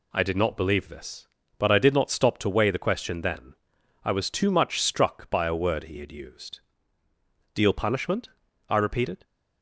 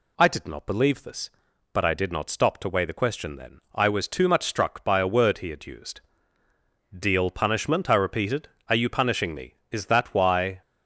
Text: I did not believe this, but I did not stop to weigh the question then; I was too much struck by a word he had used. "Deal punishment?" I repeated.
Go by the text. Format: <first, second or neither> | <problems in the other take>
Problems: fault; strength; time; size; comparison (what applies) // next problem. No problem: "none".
first | goes on to say "Are you punishing me Is that why"; strong; from 8.6 s on; 1.9 s long